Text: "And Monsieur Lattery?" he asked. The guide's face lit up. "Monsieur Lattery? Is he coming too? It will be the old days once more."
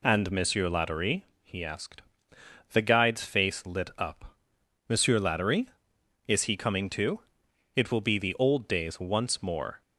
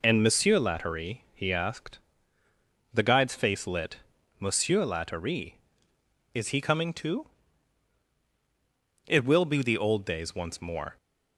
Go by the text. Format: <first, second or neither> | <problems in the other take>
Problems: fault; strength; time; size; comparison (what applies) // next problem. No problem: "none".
first | skips "up"; at 4.1 s